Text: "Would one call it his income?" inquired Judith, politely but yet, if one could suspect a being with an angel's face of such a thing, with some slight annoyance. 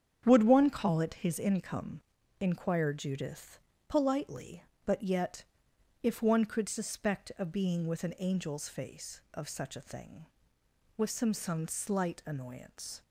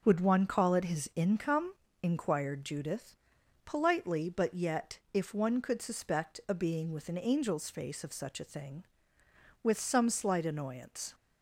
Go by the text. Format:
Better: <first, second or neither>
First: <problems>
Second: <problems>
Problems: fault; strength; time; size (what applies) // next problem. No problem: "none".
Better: second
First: starts louder than the rest; strong; until 1.2 s; 8 dB // says "some" twice; at 11.3 s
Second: starts louder than the rest; until 1.0 s; 6.5 dB